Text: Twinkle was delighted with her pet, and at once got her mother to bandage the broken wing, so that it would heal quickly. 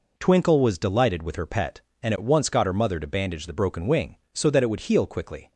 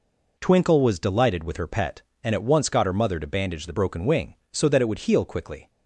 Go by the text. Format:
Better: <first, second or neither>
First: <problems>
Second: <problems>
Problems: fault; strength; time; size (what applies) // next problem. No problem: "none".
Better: neither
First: none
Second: none